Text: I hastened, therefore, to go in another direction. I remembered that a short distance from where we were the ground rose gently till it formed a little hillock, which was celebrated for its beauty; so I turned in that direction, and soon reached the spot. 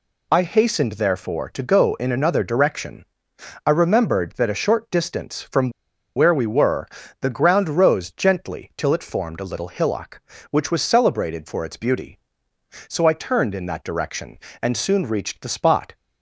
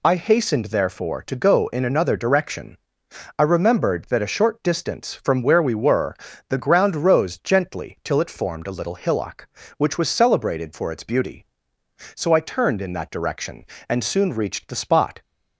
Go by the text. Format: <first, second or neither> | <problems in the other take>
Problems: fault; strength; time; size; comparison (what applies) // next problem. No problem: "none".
second | pauses between "from" and "where"; noticeable; at 5.6 s; 0.46 s long // pauses between "were" and "the"; slight; at 6.8 s; 0.36 s long; slight in the second